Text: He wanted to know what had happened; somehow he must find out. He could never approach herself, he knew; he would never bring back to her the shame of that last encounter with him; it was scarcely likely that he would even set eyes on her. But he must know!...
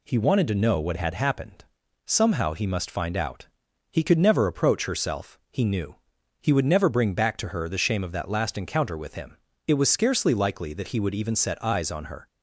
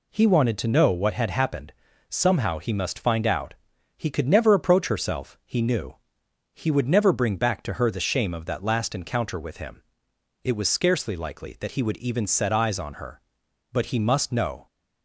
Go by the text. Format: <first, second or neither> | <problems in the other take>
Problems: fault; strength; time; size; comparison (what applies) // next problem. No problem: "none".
second | stops before "But he must know"; at 12.2 s